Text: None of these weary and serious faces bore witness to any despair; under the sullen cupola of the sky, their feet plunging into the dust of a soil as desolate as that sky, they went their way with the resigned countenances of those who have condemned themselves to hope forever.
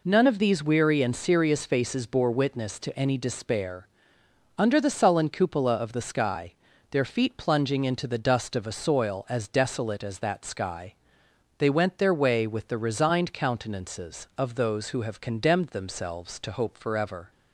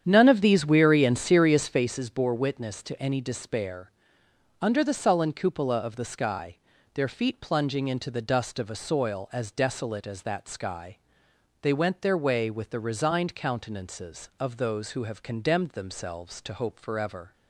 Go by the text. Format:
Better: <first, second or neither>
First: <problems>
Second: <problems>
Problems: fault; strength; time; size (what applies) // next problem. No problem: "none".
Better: first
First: none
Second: starts louder than the rest; strong; until 1.9 s; 9 dB